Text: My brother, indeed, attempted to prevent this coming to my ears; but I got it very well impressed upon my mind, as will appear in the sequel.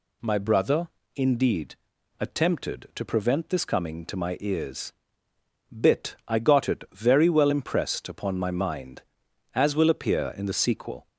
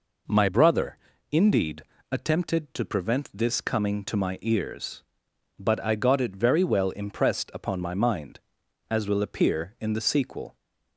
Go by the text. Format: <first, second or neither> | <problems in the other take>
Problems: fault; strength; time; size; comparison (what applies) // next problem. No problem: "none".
second | says "bit" for "but"; at 5.7 s